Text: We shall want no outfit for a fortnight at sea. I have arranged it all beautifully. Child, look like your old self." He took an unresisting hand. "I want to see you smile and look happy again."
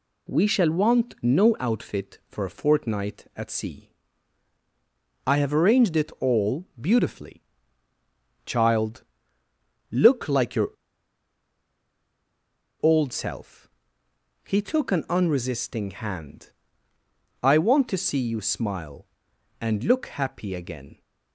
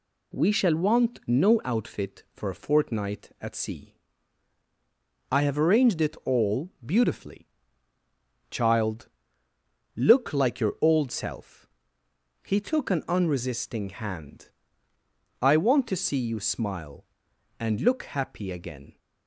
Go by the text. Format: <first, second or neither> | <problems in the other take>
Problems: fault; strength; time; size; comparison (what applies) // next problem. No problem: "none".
second | pauses between "your" and "old"; strong; at 10.6 s; 2.1 s long